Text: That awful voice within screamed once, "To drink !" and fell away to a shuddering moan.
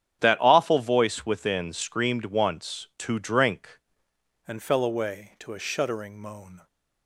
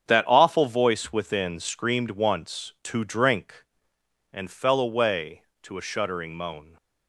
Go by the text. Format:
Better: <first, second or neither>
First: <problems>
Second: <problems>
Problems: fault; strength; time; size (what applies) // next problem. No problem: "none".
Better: second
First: starts louder than the rest; strong; until 1.2 s; 9.5 dB // changes voice at "and"; from 4.4 s on; 2.2 s long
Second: starts louder than the rest; strong; until 1.1 s; 8 dB